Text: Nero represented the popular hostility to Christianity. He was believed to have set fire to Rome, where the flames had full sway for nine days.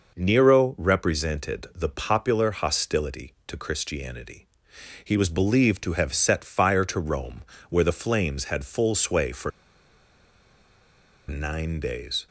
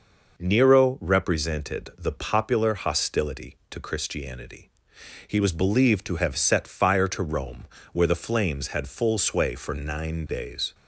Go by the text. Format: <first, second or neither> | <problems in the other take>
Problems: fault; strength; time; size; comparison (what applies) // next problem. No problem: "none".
second | pauses between "for" and "nine"; strong; at 9.5 s; 1.7 s long